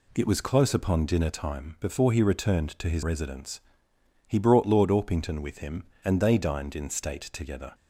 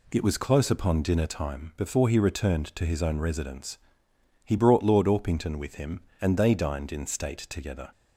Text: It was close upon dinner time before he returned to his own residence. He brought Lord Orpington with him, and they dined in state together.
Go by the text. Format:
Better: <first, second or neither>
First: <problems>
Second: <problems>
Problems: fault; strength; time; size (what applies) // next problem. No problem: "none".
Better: second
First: skips "own"; at 3.0 s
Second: none